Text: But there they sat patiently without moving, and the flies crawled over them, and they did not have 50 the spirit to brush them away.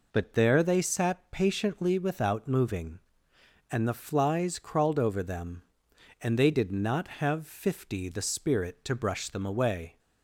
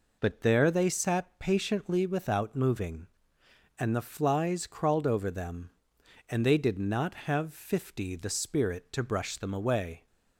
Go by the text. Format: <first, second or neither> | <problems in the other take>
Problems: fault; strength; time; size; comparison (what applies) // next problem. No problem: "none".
neither | none